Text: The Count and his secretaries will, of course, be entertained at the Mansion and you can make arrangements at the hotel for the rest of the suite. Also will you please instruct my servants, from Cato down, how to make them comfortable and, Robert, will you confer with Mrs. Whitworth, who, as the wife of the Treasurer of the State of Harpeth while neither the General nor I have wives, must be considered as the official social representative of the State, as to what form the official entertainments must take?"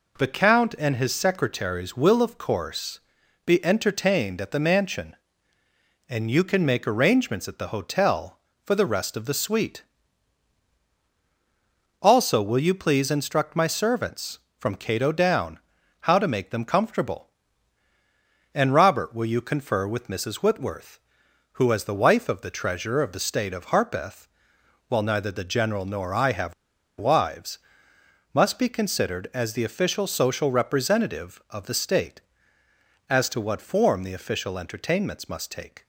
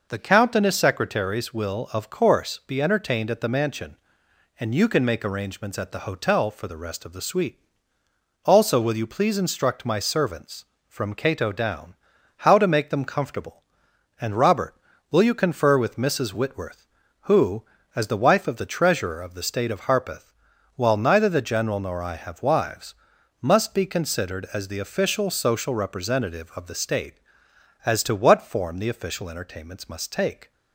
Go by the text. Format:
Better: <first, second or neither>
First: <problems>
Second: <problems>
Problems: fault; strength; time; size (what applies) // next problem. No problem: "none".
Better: second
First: pauses between "Harpeth" and "while"; noticeable; at 24.2 s; 0.60 s long // pauses between "have" and "wives"; at 26.5 s; 0.45 s long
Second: pauses between "Harpeth" and "while"; at 20.3 s; 0.42 s long